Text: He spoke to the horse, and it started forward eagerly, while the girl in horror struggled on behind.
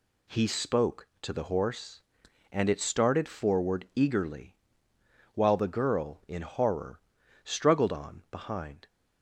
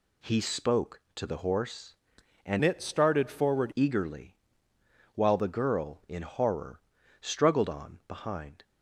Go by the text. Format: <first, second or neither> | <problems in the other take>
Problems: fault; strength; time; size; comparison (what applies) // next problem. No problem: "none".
first | changes voice from "it" to "forward"; from 2.6 to 3.7 s; 1.1 s long // pauses between "horror" and "struggled"; at 6.8 s; 0.40 s long; also in the first